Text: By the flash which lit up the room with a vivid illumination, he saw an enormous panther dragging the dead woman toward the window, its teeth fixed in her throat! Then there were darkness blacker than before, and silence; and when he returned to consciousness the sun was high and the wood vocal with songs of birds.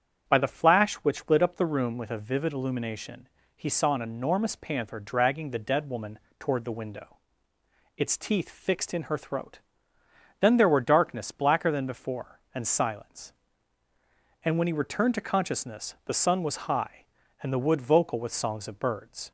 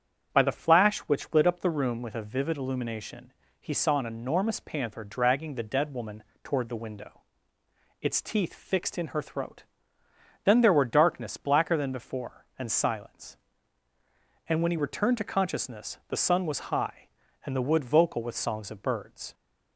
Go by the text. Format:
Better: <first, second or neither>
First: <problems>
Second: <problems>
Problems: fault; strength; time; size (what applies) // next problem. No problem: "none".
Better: neither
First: starts louder than the rest; strong; until 1.3 s; 8.5 dB // pauses between "woman" and "toward"; slight; at 6.1 s; 0.22 s long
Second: starts louder than the rest; strong; until 1.4 s; 8 dB // pauses between "woman" and "toward"; slight; at 6.2 s; 0.22 s long